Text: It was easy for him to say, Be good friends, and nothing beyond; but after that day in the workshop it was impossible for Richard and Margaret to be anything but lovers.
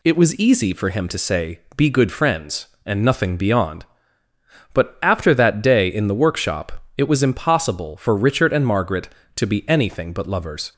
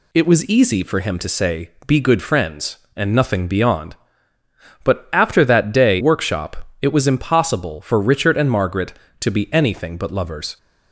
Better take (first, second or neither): first